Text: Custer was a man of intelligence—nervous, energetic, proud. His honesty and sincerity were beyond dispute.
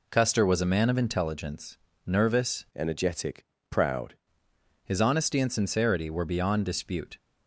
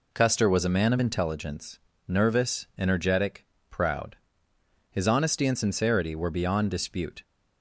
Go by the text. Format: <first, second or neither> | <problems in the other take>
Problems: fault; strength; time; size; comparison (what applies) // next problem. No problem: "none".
second | changes voice from "energetic" to "proud"; from 2.7 to 4.1 s; 1.4 s long